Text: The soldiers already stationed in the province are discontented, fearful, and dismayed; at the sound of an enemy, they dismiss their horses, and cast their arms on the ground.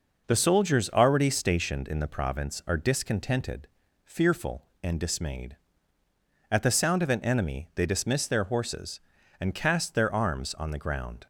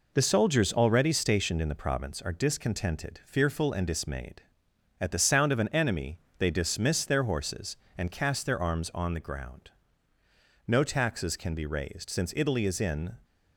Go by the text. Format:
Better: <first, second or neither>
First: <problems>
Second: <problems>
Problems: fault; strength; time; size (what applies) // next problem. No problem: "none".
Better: first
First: none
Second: goes on to say "No taxes can be raised since Italy is in"; strong; from 10.6 s on; 2.4 s long